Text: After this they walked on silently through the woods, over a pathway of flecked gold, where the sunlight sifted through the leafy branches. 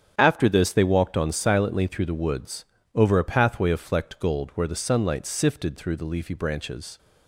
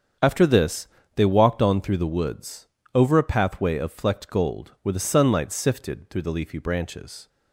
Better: first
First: starts louder than the rest; strong; until 1.1 s; 8.5 dB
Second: starts louder than the rest; strong; until 1.4 s; 7.5 dB // pauses between "this" and "they"; slight; at 0.8 s; 0.26 s long // skips "silently"; at 1.8 s

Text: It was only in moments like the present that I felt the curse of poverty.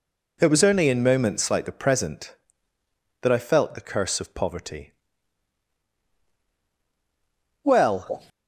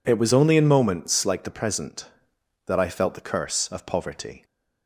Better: second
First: goes on to say "Well"; noticeable; from 7.6 s on; 0.64 s long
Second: none

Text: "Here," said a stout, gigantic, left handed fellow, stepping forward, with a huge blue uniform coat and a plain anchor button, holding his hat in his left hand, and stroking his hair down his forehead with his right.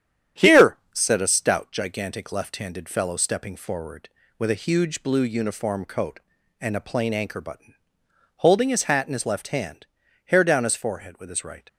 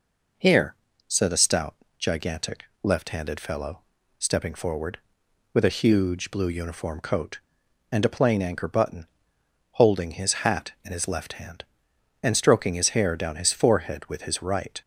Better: second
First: starts louder than the rest; strong; until 1.5 s; 9.5 dB // skips "and stroking his"; at 10.0 s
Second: none

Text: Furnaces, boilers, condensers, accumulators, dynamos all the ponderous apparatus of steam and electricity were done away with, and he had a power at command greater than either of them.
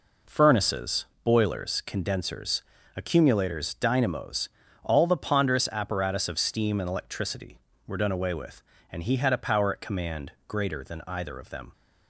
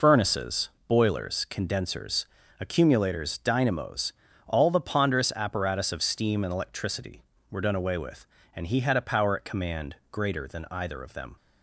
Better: first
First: pauses between "dynamos" and "all"; slight; at 4.4 s; 0.34 s long // pauses between "command" and "greater"; slight; at 10.2 s; 0.16 s long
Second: loses the start of "Furnaces"; at 0.0 s; 105 ms // pauses between "dynamos" and "all"; slight; at 4.1 s; 0.34 s long // pauses between "command" and "greater"; slight; at 9.9 s; 0.16 s long

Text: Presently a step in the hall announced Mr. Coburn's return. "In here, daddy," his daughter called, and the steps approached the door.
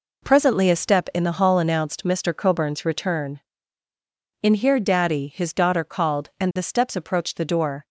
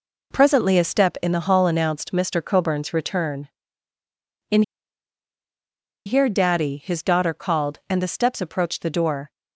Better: first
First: none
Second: pauses between "In" and "here"; strong; at 4.6 s; 1.4 s long

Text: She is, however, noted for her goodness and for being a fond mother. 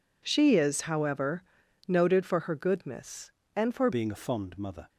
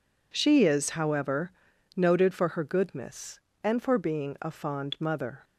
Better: second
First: changes voice at "being"; from 3.9 s on; 0.9 s long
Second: none

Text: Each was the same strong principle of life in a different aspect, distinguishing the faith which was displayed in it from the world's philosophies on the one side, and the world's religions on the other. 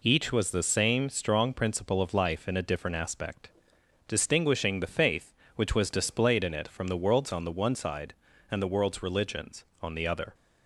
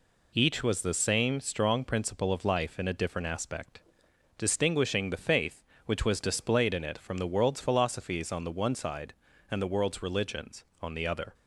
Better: second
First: skips "philosophies"; at 7.3 s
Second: none

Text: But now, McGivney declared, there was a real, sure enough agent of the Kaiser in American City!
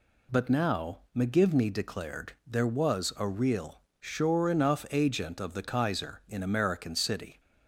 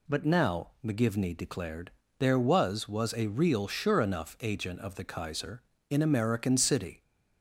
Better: first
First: none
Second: says "was" twice; at 2.8 s

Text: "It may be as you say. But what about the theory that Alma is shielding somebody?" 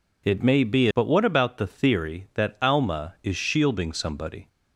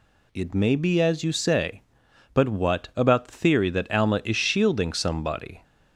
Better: second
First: skips "as you say"; at 0.9 s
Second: none

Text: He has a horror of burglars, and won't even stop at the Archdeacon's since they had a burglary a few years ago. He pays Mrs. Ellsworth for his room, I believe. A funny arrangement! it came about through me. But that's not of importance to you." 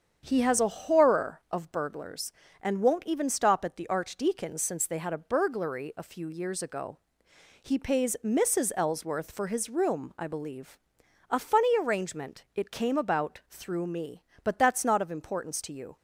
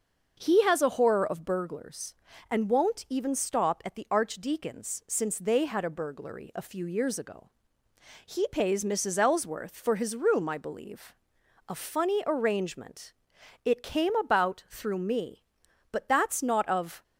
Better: first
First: starts louder than the rest; strong; until 1.2 s; 7.5 dB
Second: starts louder than the rest; until 1.3 s; 6.5 dB // stops before "importance to you"; at 17.0 s

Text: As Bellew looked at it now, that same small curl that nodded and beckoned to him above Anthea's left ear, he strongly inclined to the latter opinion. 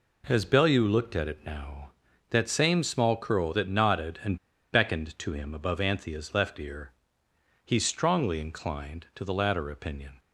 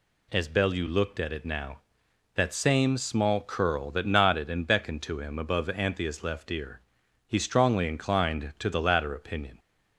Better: second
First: pauses between "and" and "beckoned"; slight; at 4.3 s; 0.34 s long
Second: none

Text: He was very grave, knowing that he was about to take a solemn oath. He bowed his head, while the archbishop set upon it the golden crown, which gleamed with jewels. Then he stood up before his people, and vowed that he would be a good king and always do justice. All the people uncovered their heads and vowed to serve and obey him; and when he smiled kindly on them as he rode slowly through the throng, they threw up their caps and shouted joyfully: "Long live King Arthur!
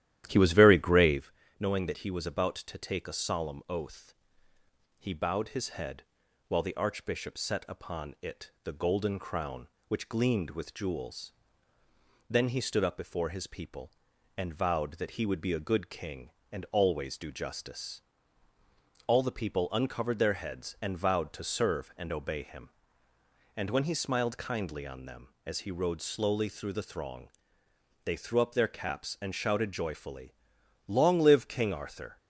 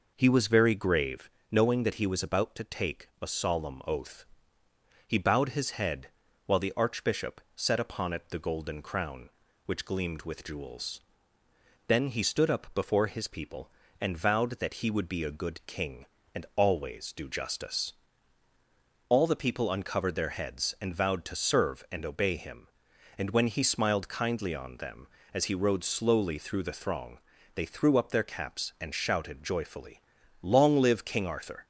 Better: second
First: starts louder than the rest; strong; until 1.2 s; 12 dB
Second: none

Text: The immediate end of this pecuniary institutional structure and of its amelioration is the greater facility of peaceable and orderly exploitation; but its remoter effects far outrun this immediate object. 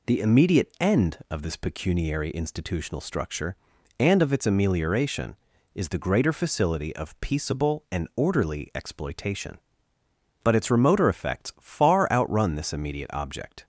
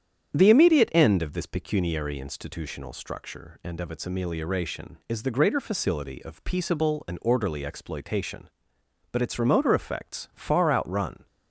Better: first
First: none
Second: starts louder than the rest; strong; until 1.4 s; 9 dB // stops before "this immediate object"; at 11.2 s

